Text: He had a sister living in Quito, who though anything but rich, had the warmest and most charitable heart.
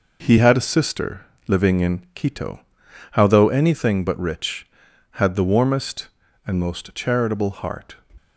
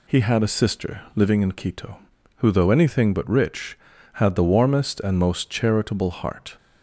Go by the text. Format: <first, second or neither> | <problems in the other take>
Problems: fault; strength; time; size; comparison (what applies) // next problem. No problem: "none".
second | pauses between "sister" and "living"; slight; at 1.2 s; 0.26 s long; slight in the second // says "how" for "who"; at 3.1 s